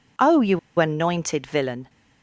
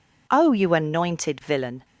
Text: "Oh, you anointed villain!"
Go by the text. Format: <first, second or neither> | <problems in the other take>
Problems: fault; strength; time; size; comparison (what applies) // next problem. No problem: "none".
second | pauses between "you" and "anointed"; slight; at 0.5 s; 0.20 s long